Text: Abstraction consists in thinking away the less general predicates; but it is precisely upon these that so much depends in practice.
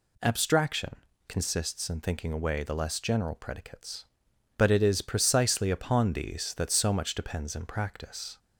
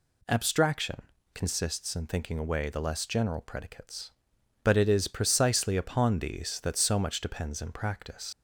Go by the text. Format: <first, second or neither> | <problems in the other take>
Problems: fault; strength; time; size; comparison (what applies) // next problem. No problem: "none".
first | pauses between "Abstraction" and "consists"; slight; at 1.0 s; 0.32 s long; slight in the first // leaves "practice" unfinished; at 8.3 s; 115 ms